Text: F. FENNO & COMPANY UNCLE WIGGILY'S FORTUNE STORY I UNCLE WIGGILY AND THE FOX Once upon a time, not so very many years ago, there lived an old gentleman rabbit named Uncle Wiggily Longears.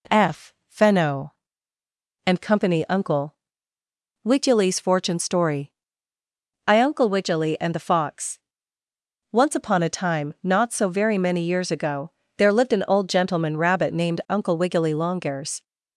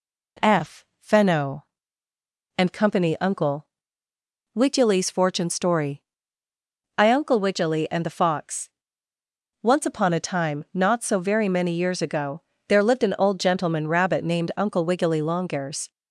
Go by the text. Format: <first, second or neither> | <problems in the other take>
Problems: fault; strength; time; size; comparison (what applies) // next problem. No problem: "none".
neither | pauses between "UNCLE" and "WIGGILY'S"; noticeable; the same in both // pauses between "STORY" and "I"; noticeable; the same in both // pauses between "FOX" and "Once"; noticeable; the same in both